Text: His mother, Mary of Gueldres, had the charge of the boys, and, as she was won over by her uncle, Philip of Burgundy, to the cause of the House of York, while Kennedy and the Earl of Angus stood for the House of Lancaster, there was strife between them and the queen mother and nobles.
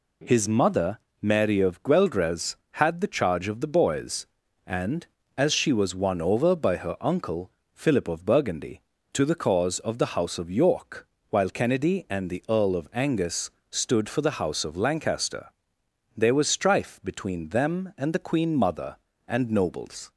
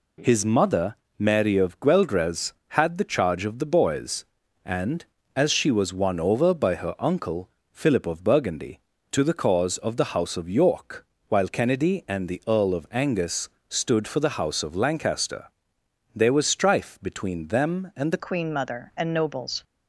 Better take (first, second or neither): first